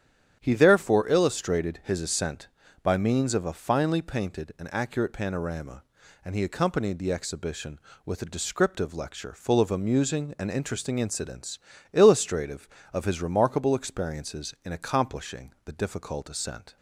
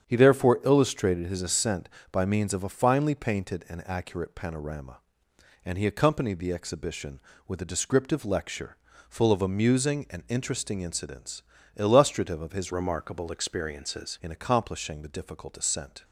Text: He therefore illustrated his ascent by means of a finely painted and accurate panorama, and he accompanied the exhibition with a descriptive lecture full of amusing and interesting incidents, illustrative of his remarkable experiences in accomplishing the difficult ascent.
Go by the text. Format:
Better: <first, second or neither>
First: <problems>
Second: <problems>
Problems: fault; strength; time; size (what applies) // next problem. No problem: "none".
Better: first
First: starts louder than the rest; strong; until 1.4 s; 9.5 dB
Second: starts louder than the rest; strong; until 1.1 s; 8.5 dB // pauses between "lecture" and "full"; slight; at 8.7 s; 0.32 s long // changes voice from "remarkable" to "experiences"; from 12.7 to 14.1 s; 1.4 s long